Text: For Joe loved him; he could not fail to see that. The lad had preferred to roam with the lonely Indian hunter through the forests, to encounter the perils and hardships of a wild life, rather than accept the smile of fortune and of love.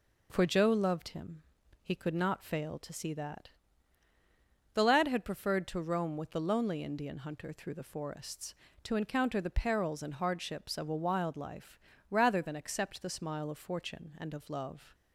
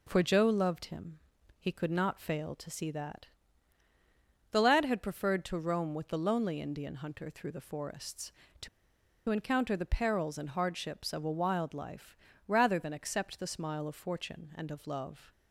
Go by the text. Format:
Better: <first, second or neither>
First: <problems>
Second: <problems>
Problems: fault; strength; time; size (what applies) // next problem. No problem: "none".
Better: first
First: none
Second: pauses between "to" and "encounter"; noticeable; at 8.6 s; 0.61 s long